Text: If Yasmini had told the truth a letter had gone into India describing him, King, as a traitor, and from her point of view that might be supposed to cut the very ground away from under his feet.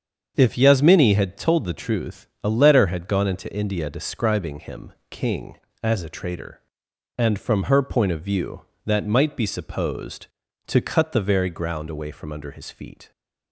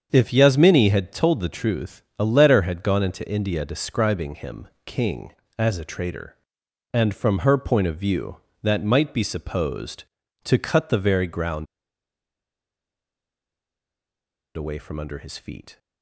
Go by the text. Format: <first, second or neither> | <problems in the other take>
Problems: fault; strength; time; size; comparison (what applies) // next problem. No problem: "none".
first | starts louder than the rest; strong; until 1.1 s; 7.5 dB; strong in the first // pauses between "truth" and "a"; slight; at 2.0 s; 0.18 s long; slight in the first // pauses between "ground" and "away"; strong; at 11.6 s; 2.9 s long